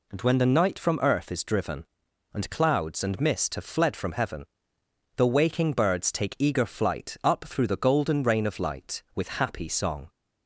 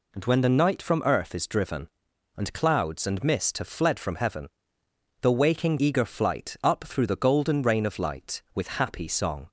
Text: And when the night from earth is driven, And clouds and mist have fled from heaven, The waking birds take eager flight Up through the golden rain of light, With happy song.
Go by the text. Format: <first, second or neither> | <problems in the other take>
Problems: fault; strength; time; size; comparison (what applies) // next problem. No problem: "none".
first | skips "birds take"; at 5.7 s